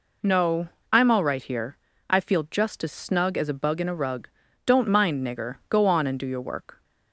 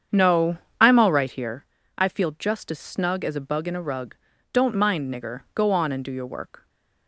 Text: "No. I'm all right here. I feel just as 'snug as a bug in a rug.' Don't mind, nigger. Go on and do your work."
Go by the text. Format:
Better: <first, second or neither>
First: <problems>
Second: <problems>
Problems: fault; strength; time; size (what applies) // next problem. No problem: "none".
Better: first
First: none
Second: starts louder than the rest; strong; until 1.4 s; 7.5 dB